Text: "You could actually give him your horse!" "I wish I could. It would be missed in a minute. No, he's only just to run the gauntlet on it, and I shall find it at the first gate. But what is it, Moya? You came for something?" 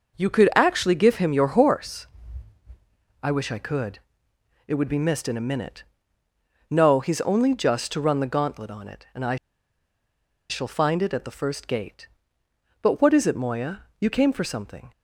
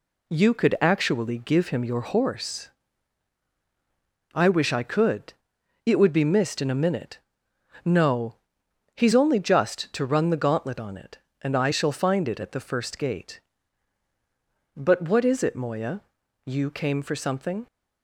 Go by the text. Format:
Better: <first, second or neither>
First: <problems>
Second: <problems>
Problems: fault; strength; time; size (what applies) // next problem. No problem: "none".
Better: second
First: pauses between "I" and "shall"; at 9.3 s; 1.1 s long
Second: none